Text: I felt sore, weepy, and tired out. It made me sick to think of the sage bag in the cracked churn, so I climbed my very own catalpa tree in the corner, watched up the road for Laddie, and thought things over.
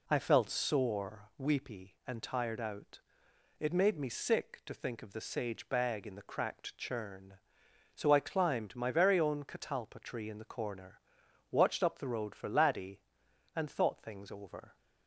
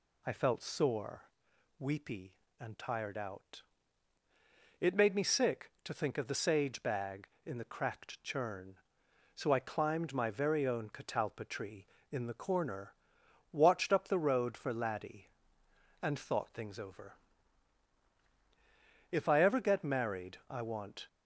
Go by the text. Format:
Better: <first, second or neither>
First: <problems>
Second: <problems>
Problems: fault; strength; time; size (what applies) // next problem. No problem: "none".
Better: first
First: none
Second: goes on to say "If I ever get married I want"; strong; from 19.1 s on; 1.9 s long